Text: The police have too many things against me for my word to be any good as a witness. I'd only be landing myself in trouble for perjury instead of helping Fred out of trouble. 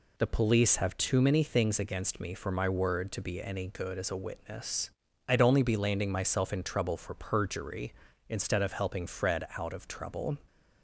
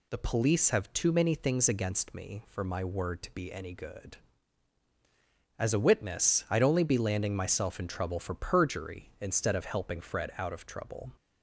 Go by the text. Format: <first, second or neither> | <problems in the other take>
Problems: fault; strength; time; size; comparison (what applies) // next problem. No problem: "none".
neither | none